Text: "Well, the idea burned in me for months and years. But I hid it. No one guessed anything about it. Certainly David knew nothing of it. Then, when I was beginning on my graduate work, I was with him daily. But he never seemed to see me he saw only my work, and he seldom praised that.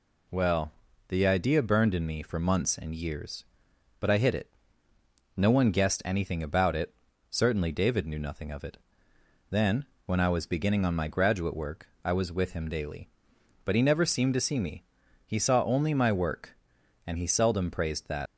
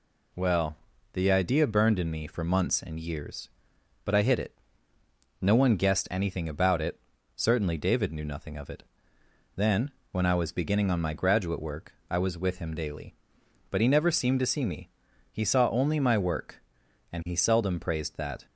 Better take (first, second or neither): second